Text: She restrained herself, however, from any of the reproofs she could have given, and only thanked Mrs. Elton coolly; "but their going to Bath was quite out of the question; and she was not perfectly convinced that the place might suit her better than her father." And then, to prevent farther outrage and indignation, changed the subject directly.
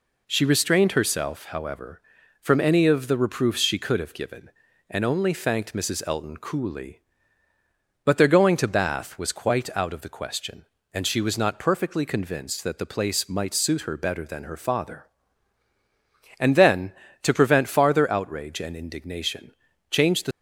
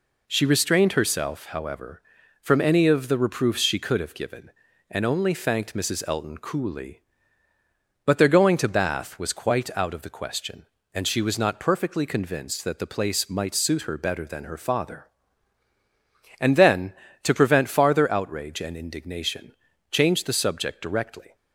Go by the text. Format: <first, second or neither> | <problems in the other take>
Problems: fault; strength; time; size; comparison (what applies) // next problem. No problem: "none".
second | stops before "subject directly"; at 20.3 s